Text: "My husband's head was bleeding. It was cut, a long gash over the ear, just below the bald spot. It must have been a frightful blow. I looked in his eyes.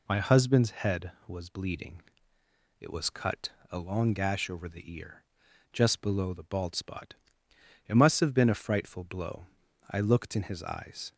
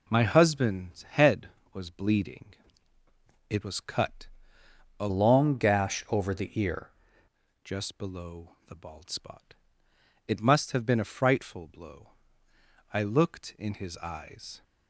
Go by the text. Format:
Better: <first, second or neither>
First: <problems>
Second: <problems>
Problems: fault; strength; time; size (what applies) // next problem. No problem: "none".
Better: first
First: none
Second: changes voice from "long" to "ear"; from 5.0 to 6.9 s; 1.9 s long